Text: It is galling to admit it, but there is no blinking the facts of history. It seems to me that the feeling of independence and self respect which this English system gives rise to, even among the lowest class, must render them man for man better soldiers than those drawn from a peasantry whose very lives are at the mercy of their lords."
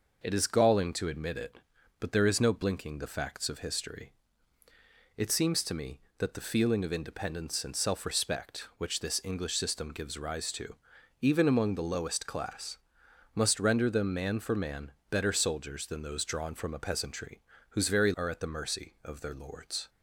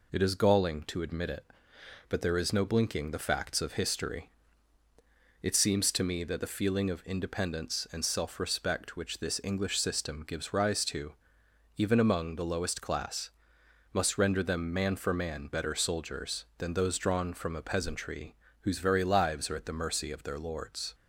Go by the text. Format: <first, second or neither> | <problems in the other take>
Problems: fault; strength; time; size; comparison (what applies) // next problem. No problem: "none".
second | pauses between "man" and "better"; slight; at 14.9 s; 0.18 s long // pauses between "peasantry" and "whose"; slight; at 17.4 s; 0.30 s long; slight in the second // skips "lives"; at 18.1 s